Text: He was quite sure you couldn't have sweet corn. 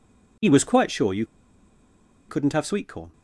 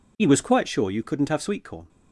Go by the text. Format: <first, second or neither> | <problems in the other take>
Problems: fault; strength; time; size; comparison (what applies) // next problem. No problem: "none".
second | pauses between "you" and "couldn't"; at 1.2 s; 1.0 s long